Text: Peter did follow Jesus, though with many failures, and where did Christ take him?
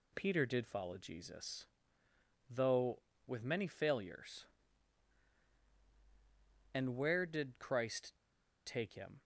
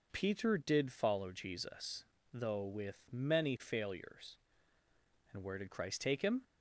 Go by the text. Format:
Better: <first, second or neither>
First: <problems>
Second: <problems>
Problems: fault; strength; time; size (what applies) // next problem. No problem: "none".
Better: second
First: pauses between "Christ" and "take"; noticeable; at 8.1 s; 0.53 s long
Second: none